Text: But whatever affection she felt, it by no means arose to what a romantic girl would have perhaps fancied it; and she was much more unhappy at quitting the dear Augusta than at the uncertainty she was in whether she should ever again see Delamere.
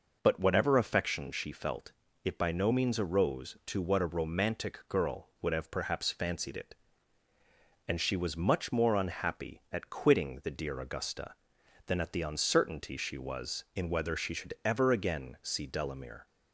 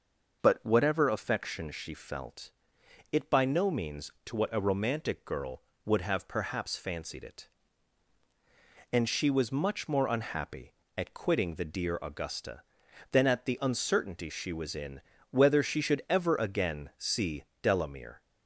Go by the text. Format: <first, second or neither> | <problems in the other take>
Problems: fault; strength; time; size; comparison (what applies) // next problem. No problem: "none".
first | starts louder than the rest; noticeable; until 1.4 s; 6 dB // skips "arose"; at 4.1 s // pauses between "in" and "whether"; slight; at 15.0 s; 0.30 s long // pauses between "see" and "Delamere"; slight; at 17.4 s; 0.18 s long